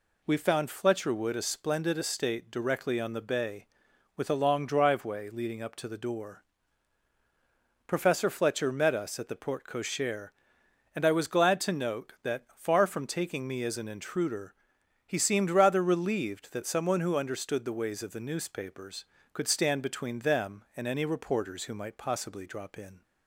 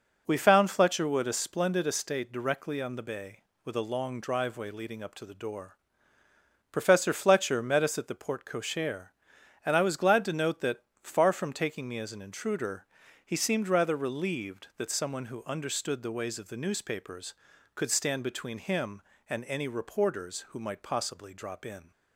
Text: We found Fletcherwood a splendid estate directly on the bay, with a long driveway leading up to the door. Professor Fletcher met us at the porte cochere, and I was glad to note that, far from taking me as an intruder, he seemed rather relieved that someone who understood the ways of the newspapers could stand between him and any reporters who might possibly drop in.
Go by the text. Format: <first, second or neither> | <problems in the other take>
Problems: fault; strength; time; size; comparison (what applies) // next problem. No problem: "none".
second | says "them" for "him"; at 20.2 s